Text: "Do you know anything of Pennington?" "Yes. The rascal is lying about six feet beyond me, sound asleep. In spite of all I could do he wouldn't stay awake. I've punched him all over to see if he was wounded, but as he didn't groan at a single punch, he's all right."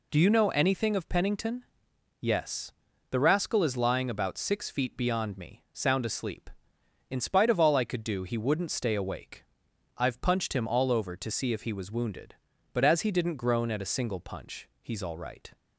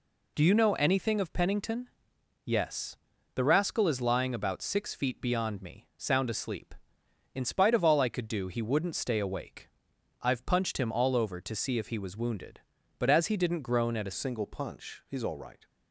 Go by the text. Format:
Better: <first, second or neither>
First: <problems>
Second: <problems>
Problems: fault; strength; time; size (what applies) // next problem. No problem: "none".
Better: first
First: none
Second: changes voice at "single"; from 14.1 s on; 1.5 s long